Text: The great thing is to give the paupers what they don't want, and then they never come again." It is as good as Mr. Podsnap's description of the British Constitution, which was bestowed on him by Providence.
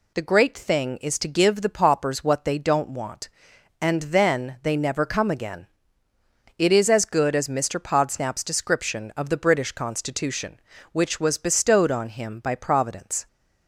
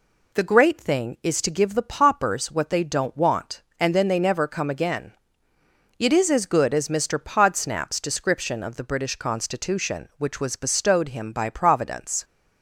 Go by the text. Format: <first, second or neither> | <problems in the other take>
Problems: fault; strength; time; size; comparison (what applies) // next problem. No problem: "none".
first | skips "on"; at 11.0 s